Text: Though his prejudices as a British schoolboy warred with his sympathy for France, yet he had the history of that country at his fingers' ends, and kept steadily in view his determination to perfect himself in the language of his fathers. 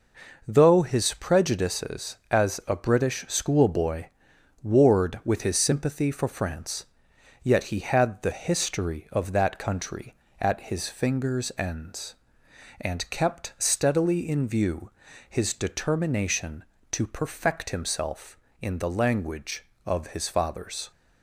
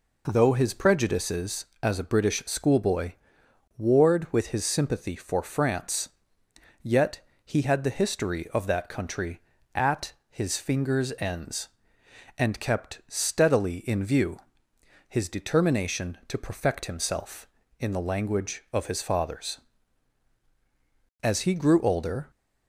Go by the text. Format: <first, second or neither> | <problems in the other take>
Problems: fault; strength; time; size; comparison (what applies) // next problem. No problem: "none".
first | pauses between "schoolboy" and "warred"; noticeable; at 3.1 s; 0.66 s long; noticeable in the first // pauses between "yet" and "he"; slight; at 7.2 s; 0.24 s long // pauses between "view" and "his"; noticeable; at 14.3 s; 0.70 s long; also in the first // goes on to say "As he grew older"; noticeable; from 21.2 s on; 1.0 s long